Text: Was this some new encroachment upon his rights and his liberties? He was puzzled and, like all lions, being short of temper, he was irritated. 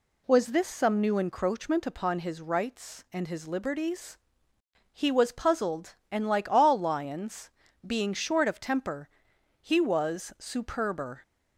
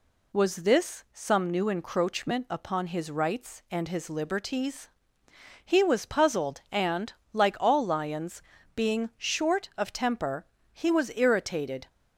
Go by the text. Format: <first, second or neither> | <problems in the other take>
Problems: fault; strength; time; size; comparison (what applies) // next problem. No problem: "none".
second | says "superber" for "irritated"; at 10.3 s